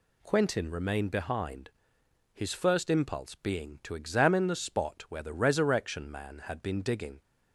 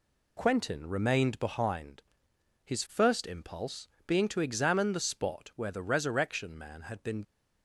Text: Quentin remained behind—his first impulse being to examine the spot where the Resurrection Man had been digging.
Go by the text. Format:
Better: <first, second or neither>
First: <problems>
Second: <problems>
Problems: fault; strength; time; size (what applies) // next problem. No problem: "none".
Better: first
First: none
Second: pauses between "impulse" and "being"; slight; at 3.8 s; 0.18 s long // stops before "digging"; at 7.2 s